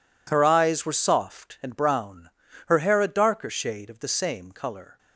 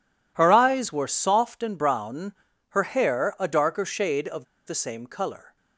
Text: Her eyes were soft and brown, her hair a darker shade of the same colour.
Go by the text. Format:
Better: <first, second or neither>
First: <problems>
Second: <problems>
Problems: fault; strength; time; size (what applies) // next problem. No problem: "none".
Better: first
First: none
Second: pauses between "of" and "the"; slight; at 4.4 s; 0.22 s long